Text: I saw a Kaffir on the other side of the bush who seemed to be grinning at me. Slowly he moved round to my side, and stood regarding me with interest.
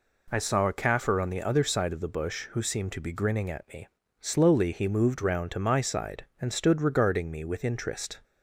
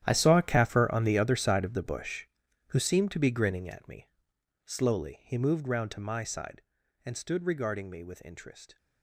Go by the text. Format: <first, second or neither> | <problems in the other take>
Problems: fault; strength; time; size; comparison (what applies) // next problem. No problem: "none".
first | gets quieter; strong; throughout; 16 dB